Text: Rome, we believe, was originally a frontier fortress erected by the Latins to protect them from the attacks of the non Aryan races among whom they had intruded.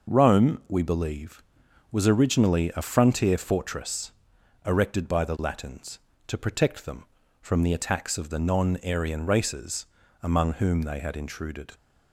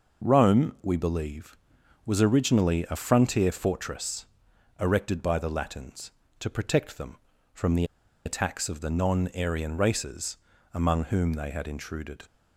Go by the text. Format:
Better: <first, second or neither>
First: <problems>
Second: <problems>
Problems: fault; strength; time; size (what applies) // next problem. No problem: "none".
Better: first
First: pauses between "fortress" and "erected"; noticeable; at 4.1 s; 0.54 s long // pauses between "races" and "among"; slight; at 9.8 s; 0.34 s long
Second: pauses between "fortress" and "erected"; noticeable; at 4.2 s; 0.54 s long // pauses between "the" and "attacks"; at 7.8 s; 0.40 s long // pauses between "races" and "among"; slight; at 10.3 s; 0.34 s long